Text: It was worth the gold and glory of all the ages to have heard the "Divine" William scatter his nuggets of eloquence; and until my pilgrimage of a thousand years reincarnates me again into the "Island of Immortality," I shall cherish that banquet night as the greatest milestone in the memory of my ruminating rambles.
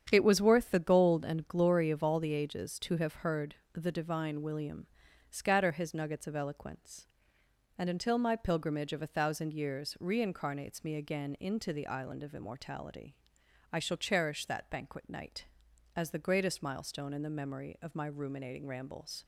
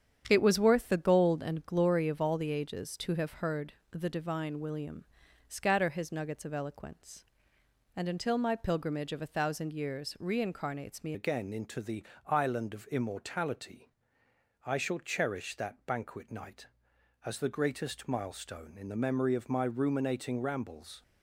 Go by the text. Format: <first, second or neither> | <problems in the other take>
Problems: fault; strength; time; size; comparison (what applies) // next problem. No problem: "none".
first | starts louder than the rest; strong; until 1.2 s; 8.5 dB; strong in the first // pauses between "heard" and "the"; slight; at 3.7 s; 0.18 s long; slight in the first // pauses between "William" and "scatter"; at 5.0 s; 0.42 s long; also in the first // changes voice at "again"; from 11.1 s on; 9.9 s long // pauses between "the" and "Island"; slight; at 12.0 s; 0.22 s long